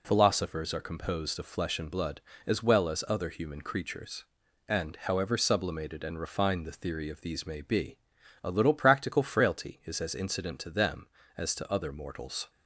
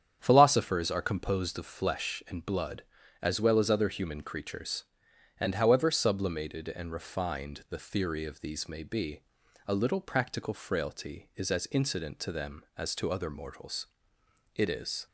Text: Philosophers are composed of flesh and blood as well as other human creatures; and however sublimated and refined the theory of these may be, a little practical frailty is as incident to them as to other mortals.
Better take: first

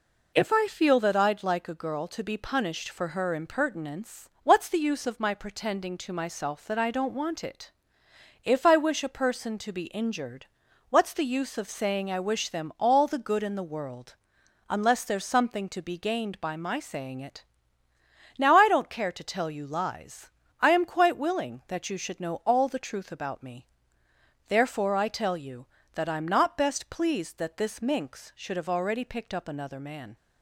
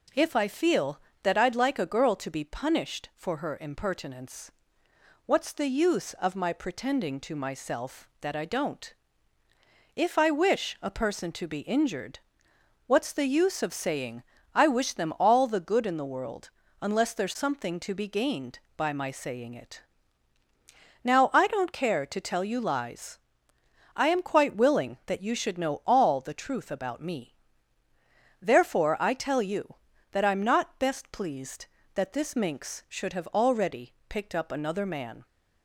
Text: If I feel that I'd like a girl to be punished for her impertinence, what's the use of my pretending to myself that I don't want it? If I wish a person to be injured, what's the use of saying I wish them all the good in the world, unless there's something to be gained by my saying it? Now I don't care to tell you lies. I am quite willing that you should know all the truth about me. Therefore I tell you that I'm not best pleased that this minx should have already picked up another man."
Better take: first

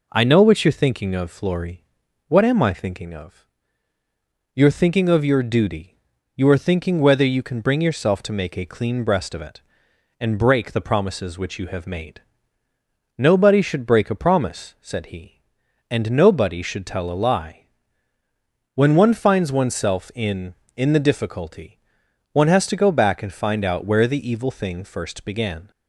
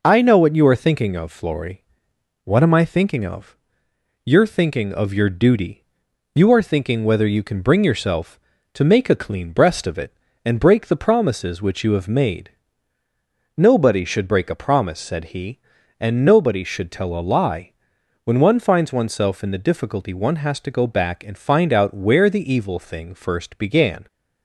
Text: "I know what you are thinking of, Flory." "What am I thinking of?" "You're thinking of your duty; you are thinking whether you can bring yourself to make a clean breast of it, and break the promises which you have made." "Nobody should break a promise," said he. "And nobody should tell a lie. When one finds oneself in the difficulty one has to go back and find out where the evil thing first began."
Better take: second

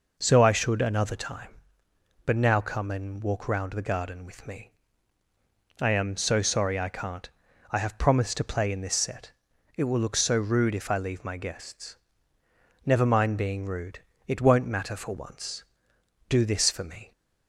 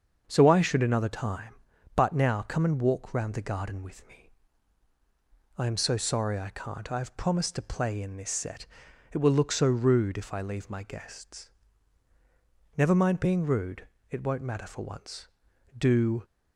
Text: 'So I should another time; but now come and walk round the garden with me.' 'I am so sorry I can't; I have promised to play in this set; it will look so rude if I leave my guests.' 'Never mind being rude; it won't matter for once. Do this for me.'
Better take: first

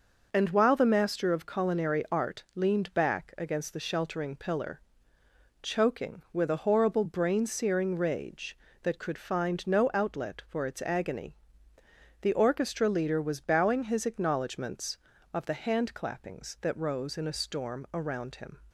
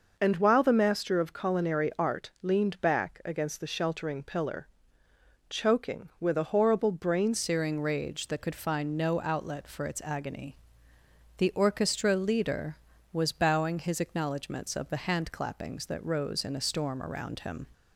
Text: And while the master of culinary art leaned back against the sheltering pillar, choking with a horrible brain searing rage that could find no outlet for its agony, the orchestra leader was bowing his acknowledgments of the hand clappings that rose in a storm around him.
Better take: first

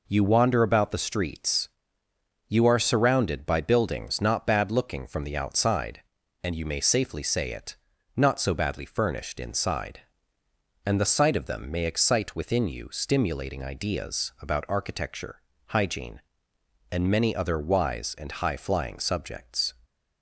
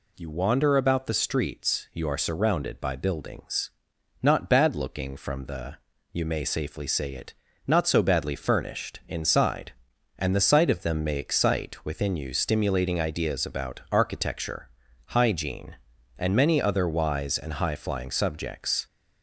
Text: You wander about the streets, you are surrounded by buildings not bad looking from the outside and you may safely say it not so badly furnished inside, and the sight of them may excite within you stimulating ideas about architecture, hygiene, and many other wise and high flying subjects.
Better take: first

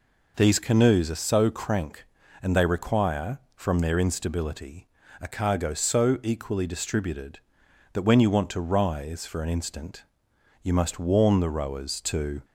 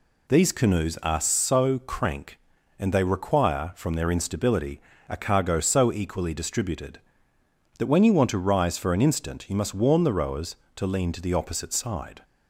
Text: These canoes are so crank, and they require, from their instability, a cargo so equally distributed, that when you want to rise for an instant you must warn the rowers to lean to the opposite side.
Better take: second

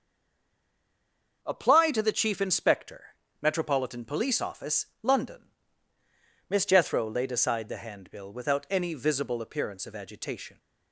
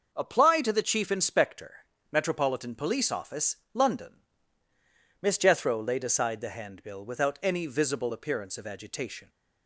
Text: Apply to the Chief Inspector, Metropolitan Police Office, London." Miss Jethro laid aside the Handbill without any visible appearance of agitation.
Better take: second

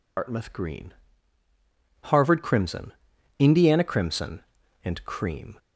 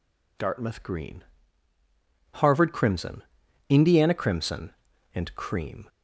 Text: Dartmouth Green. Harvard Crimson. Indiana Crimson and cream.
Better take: second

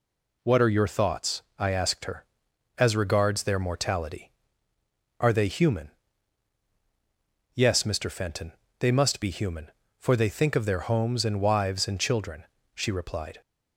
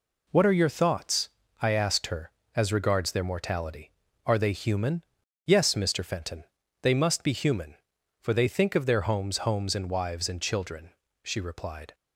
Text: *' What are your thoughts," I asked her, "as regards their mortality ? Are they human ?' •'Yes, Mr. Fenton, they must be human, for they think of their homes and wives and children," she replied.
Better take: first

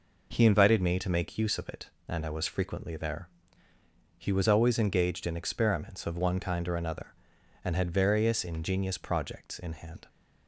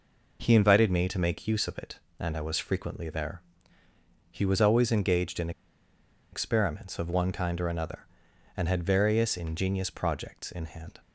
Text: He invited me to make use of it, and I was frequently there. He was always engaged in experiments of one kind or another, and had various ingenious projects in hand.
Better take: first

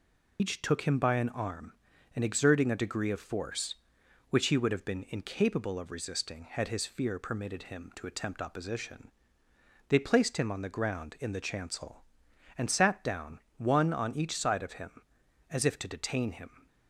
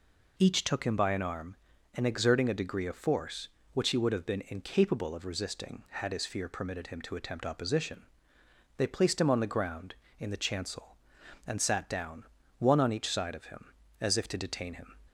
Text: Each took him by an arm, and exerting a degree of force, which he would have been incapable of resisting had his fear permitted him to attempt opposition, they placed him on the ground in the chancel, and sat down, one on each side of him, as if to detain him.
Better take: second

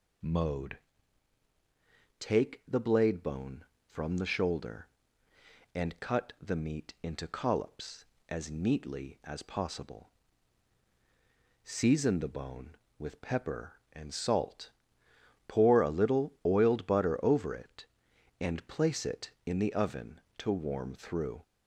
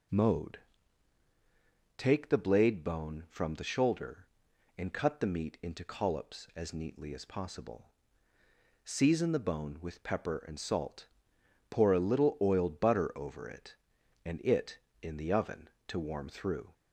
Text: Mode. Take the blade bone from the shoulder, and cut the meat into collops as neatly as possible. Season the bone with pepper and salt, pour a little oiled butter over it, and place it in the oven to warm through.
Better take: first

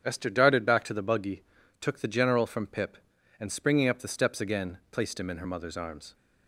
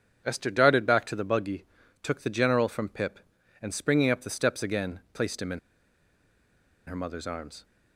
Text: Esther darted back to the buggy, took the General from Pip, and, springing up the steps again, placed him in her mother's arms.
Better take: first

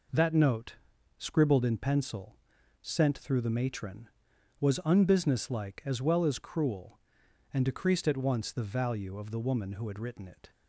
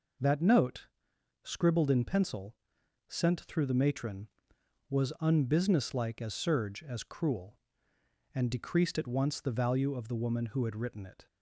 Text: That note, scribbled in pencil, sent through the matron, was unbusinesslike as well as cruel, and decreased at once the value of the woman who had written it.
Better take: first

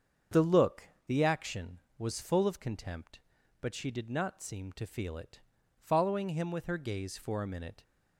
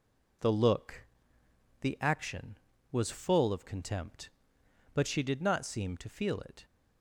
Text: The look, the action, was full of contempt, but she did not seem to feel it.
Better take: second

